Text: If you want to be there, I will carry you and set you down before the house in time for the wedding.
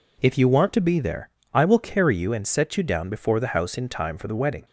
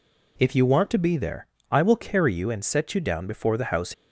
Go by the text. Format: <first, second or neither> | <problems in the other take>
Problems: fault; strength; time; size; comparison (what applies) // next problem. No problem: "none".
first | stops before "in time for the wedding"; at 3.9 s